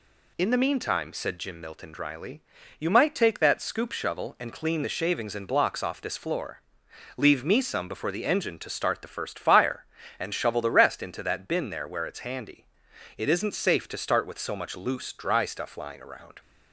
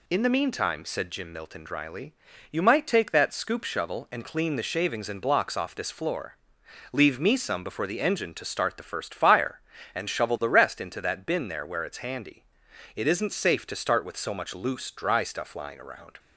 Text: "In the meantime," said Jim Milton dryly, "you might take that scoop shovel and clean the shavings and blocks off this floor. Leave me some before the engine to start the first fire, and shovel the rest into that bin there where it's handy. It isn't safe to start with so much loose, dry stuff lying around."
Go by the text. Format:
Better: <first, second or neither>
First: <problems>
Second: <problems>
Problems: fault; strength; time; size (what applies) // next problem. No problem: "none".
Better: neither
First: none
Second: none